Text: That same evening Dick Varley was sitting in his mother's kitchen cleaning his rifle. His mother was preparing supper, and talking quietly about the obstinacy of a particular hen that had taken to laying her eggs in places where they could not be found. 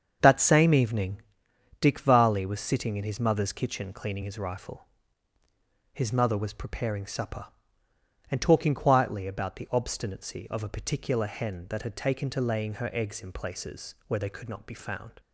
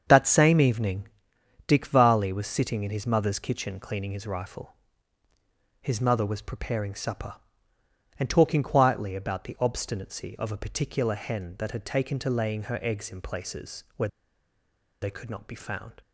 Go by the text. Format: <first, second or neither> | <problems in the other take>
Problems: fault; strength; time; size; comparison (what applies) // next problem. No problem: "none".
first | starts louder than the rest; strong; until 1.0 s; 7 dB; strong in the first // pauses between "evening" and "Dick"; noticeable; at 1.0 s; 0.58 s long; noticeable in the first // pauses between "where" and "they"; noticeable; at 14.0 s; 0.93 s long